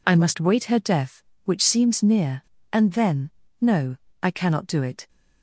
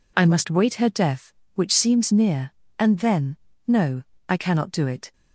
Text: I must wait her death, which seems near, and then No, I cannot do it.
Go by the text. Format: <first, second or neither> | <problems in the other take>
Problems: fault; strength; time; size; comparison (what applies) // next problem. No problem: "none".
neither | pauses between "then" and "No"; slight; the same in both